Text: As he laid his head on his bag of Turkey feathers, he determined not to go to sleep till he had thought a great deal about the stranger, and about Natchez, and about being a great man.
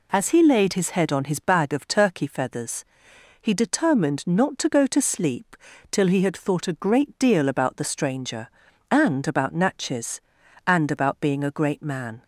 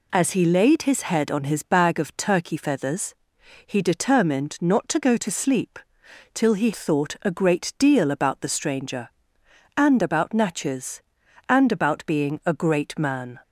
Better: first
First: pauses between "sleep" and "till"; slight; at 5.5 s; 0.36 s long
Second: pauses between "sleep" and "till"; noticeable; at 5.7 s; 0.56 s long // skips "had"; at 6.7 s

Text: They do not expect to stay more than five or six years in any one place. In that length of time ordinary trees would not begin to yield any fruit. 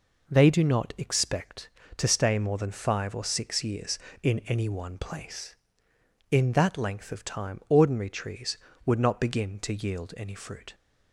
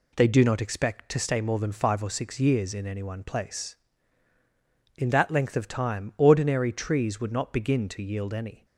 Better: first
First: none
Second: stops before "fruit"; at 8.6 s

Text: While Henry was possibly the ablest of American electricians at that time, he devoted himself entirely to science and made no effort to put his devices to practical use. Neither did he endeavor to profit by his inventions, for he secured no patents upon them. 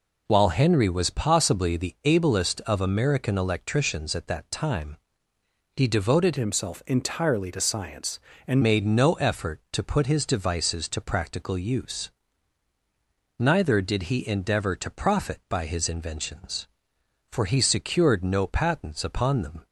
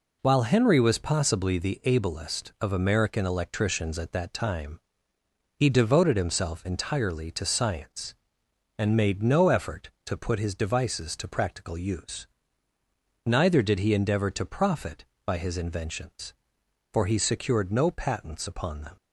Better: second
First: changes voice from "himself" to "and"; from 6.3 to 8.6 s; 2.3 s long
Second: none

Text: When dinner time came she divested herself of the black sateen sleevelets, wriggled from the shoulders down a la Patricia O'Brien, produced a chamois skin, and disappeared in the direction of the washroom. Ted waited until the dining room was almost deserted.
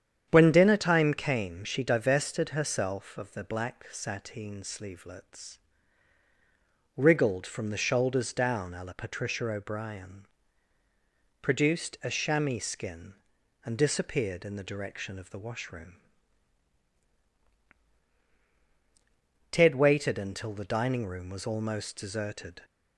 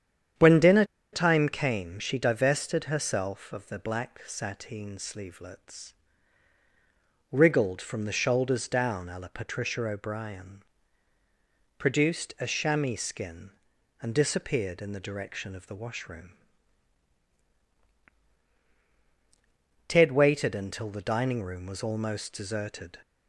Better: first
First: starts louder than the rest; strong; until 1.3 s; 9 dB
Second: starts louder than the rest; strong; until 1.6 s; 9 dB // pauses between "dinner" and "time"; slight; at 0.8 s; 0.28 s long

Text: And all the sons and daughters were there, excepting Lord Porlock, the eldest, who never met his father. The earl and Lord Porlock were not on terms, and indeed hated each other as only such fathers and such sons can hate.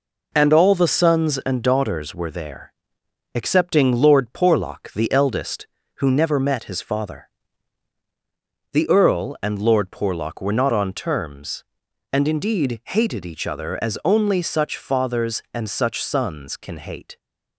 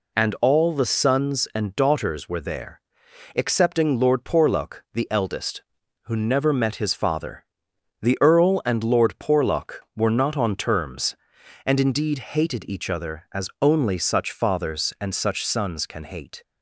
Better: neither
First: none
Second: none

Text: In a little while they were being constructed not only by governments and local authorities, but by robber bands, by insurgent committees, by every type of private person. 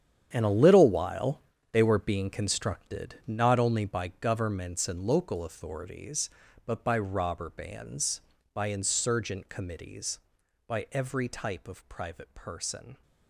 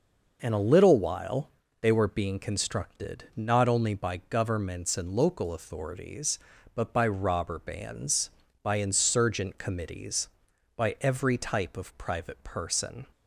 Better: second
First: gets quieter; strong; throughout; 13 dB // pauses between "while" and "they"; slight; at 1.4 s; 0.30 s long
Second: pauses between "while" and "they"; slight; at 1.5 s; 0.30 s long

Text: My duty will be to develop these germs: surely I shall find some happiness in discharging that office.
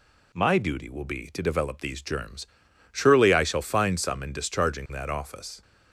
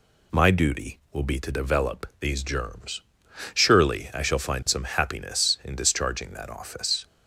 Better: second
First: skips "happiness"; at 4.2 s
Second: none

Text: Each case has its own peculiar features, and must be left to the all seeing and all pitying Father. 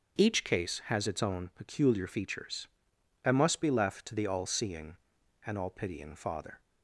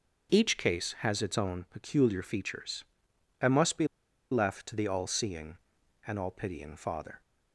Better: first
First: starts louder than the rest; until 1.2 s; 7 dB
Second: starts louder than the rest; until 1.3 s; 6.5 dB // pauses between "be" and "left"; at 3.8 s; 0.45 s long

